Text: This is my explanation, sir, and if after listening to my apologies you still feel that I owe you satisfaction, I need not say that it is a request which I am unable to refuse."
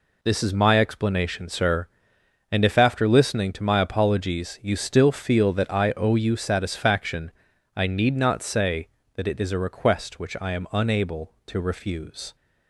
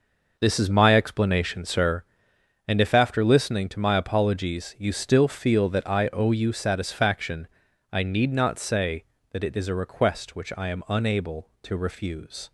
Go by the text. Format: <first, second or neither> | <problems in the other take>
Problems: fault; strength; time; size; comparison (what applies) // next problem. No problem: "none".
first | starts louder than the rest; noticeable; until 1.9 s; 5.5 dB